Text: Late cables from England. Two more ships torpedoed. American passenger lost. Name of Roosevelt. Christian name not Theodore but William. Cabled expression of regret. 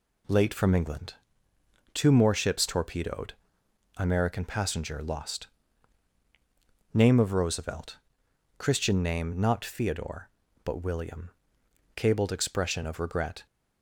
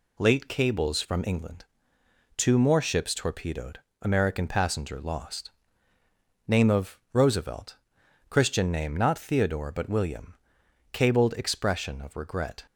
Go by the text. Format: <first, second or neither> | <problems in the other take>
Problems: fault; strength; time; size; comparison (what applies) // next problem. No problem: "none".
second | skips "cables"; at 0.5 s